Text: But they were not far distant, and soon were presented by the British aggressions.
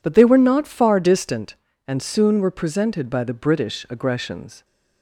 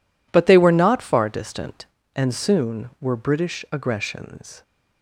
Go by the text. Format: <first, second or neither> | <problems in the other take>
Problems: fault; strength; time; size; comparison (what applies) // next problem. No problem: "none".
first | skips "presented by the"; at 3.1 s